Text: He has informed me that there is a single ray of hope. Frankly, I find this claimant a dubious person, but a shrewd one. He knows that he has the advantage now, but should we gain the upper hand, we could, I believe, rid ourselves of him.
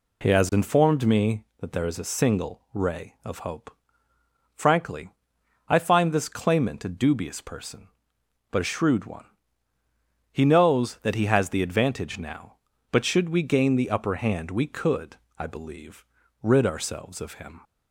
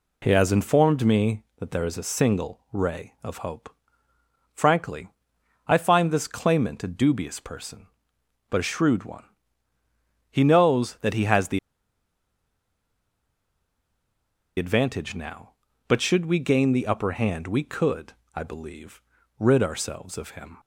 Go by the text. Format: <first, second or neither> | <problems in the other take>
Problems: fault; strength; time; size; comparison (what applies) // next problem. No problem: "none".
first | pauses between "the" and "advantage"; strong; at 11.5 s; 2.9 s long